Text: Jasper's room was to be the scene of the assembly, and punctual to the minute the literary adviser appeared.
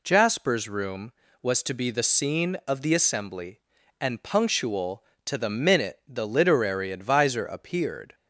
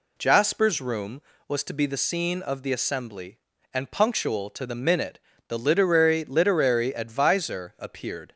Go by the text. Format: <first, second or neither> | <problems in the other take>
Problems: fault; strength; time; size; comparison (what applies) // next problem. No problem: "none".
first | pauses between "minute" and "the"; slight; at 5.1 s; 0.28 s long // says "literary" twice; at 6.2 s